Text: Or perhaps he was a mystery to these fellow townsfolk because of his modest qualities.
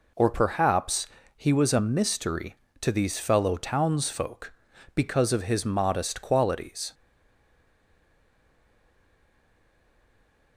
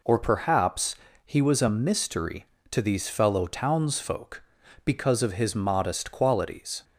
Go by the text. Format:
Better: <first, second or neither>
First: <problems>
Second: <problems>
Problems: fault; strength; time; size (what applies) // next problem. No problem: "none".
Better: second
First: pauses between "perhaps" and "he"; slight; at 1.0 s; 0.30 s long // stays silent after the last word; strong; from 6.9 s on; 3.6 s long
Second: pauses between "perhaps" and "he"; slight; at 0.9 s; 0.30 s long